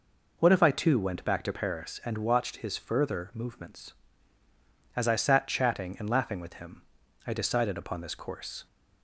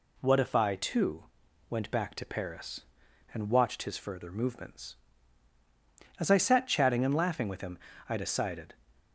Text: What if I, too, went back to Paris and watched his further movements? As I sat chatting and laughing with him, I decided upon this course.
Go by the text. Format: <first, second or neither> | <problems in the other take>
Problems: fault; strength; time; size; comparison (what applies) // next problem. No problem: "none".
first | stops before "upon this course"; at 9.0 s